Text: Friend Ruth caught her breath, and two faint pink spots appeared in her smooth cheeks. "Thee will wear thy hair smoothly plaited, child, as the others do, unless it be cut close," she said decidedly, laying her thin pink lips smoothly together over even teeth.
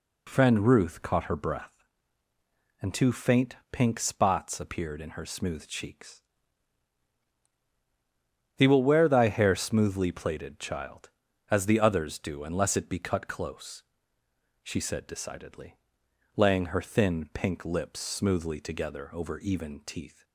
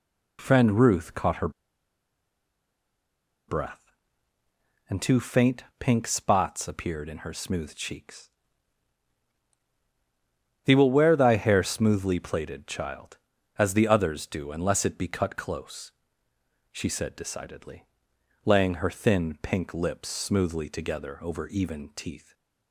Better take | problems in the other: first | pauses between "her" and "breath"; strong; at 1.4 s; 1.9 s long // pauses between "faint" and "pink"; slight; at 5.6 s; 0.16 s long; slight in the first

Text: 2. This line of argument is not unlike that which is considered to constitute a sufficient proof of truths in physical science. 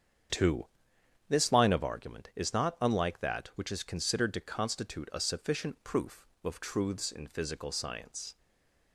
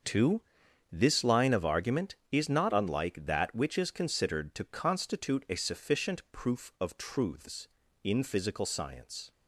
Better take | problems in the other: second | starts louder than the rest; strong; until 1.9 s; 8 dB; also in the second // stays silent after the last word; slight; from 8.3 s on; 0.6 s long

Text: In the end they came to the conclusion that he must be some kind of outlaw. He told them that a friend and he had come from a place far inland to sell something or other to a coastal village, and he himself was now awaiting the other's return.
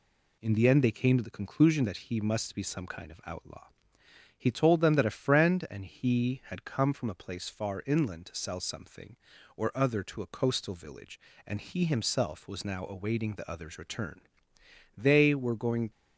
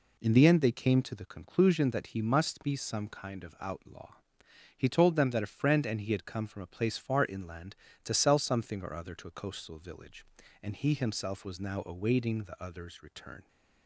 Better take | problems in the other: second | goes on to say "They were going"; noticeable; from 14.9 s on; 0.94 s long

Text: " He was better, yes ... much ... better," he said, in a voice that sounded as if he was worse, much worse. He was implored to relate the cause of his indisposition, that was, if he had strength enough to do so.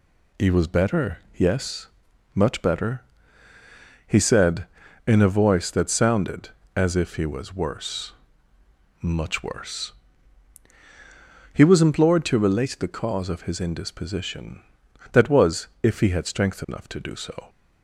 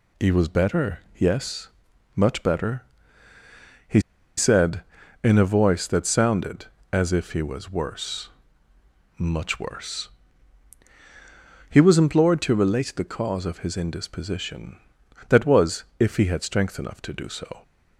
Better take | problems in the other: first | pauses between "he" and "said"; at 3.9 s; 0.38 s long

